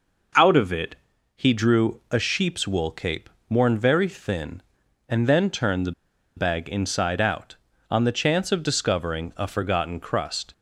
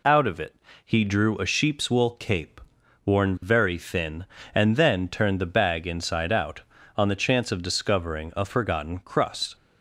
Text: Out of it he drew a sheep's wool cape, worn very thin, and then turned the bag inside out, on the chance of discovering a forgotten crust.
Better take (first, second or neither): second